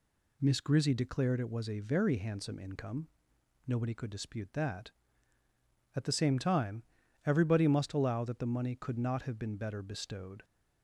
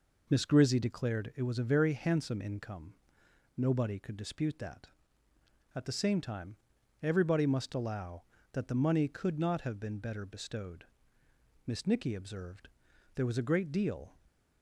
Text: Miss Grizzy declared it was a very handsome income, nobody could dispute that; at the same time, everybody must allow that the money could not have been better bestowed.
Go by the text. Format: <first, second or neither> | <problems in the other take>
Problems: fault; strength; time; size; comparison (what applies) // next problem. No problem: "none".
first | goes on to say "Miss Nicky observed there was a great deal"; strong; from 11.6 s on; 2.5 s long